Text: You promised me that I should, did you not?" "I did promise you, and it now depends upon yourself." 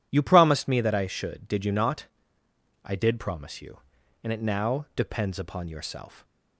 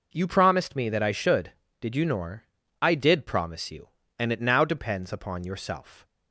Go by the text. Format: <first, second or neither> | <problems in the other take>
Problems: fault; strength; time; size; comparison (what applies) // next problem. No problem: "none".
first | says "nor" for "not"; at 2.0 s